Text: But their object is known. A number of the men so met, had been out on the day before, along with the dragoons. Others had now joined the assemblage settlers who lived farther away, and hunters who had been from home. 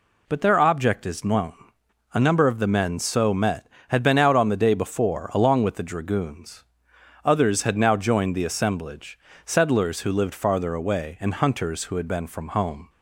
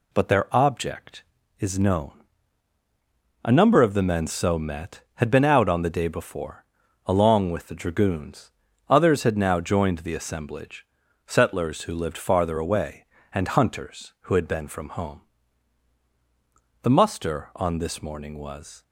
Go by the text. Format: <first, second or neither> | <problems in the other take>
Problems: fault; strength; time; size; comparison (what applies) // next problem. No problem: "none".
first | pauses between "assemblage" and "settlers"; at 10.8 s; 0.42 s long; slight in the first // goes on to say "The muster on this morning was"; strong; from 16.8 s on; 2.0 s long